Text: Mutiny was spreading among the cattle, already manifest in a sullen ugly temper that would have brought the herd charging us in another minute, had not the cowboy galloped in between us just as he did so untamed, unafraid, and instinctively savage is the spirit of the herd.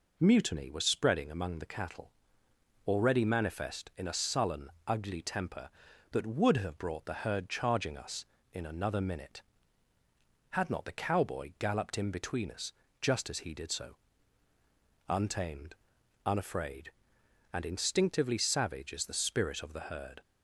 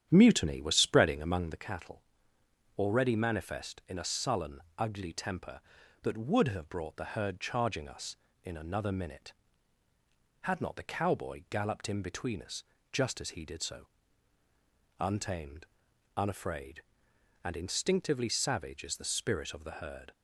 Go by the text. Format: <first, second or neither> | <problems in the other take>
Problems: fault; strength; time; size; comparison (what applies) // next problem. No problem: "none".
first | starts louder than the rest; strong; until 1.7 s; 10 dB // pauses between "sullen" and "ugly"; slight; at 4.5 s; 0.18 s long; slight in the first // pauses between "us" and "just"; slight; at 12.6 s; 0.30 s long; slight in the first // pauses between "so" and "untamed"; at 13.8 s; 1.1 s long; also in the first